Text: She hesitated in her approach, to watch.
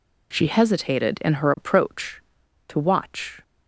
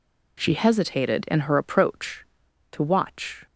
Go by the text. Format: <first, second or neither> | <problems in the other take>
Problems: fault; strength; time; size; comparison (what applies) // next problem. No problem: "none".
neither | none